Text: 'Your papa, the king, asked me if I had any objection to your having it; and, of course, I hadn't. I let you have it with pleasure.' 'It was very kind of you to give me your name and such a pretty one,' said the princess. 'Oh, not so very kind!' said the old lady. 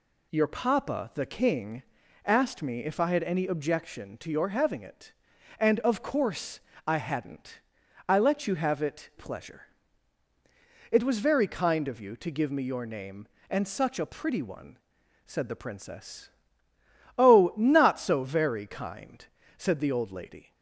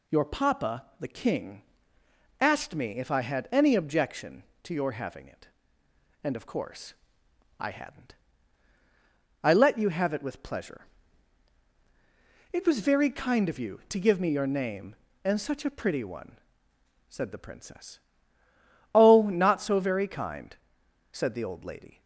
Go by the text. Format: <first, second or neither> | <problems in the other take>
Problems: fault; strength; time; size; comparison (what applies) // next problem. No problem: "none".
second | skips "with"; at 9.1 s